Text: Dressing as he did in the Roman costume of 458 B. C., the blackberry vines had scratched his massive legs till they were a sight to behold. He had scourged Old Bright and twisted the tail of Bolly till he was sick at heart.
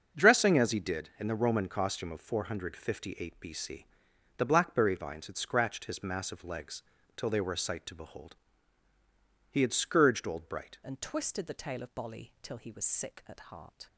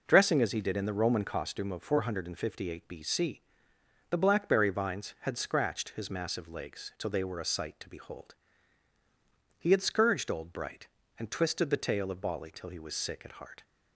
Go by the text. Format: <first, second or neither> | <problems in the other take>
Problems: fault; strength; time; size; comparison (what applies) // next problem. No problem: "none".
second | starts louder than the rest; until 1.2 s; 6.5 dB // pauses between "legs" and "till"; slight; at 6.8 s; 0.34 s long // changes voice at "and"; from 10.8 s on; 3.0 s long